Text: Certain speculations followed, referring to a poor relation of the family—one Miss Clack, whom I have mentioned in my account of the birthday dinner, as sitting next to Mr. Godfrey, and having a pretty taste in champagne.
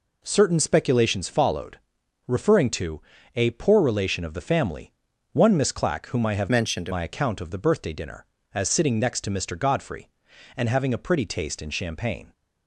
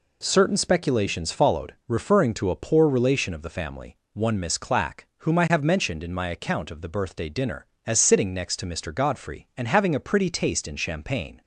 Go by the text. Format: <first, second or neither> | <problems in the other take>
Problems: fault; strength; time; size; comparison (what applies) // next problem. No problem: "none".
second | pauses between "to" and "a"; slight; at 3.0 s; 0.32 s long // changes voice from "mentioned" to "in"; from 6.4 to 6.8 s; 0.4 s long